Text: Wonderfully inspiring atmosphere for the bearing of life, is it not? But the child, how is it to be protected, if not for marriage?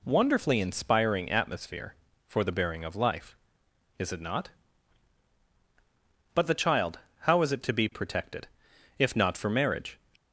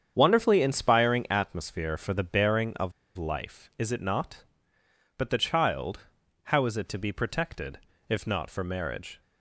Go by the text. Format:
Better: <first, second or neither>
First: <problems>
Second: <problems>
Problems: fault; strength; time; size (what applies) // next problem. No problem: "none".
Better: first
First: none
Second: starts louder than the rest; strong; until 1.1 s; 8 dB // pauses between "of" and "life"; slight; at 2.9 s; 0.25 s long